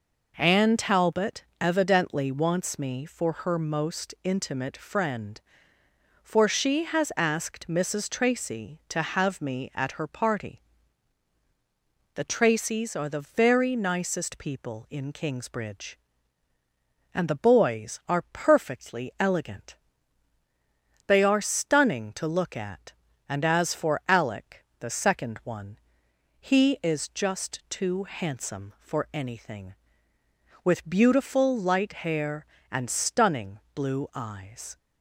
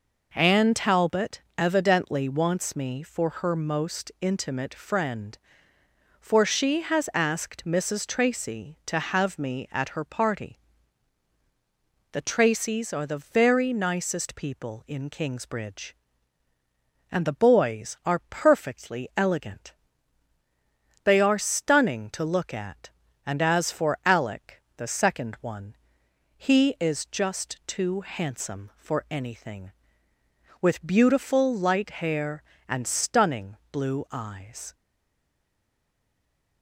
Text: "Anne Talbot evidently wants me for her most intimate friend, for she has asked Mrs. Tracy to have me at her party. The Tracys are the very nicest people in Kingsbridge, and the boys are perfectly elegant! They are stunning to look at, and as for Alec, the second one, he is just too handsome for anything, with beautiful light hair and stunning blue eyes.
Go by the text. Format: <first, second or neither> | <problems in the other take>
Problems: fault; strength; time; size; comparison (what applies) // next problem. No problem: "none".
first | pauses between "Talbot" and "evidently"; slight; at 1.4 s; 0.16 s long; slight in the first // pauses between "stunning" and "blue"; slight; at 33.5 s; 0.16 s long; slight in the first // stays silent after the last word; noticeable; from 34.7 s on; 1.9 s long